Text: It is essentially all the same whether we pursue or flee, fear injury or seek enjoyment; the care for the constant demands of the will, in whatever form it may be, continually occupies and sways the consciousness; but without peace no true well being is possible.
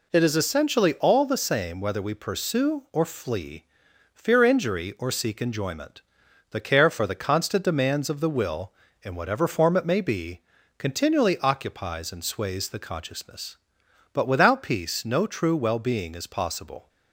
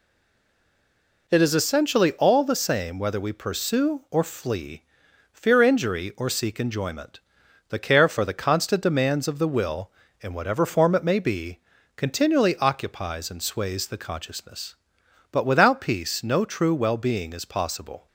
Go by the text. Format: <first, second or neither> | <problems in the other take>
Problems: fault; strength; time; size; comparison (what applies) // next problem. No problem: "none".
first | stays silent before the first word; noticeable; until 1.2 s; 1.2 s long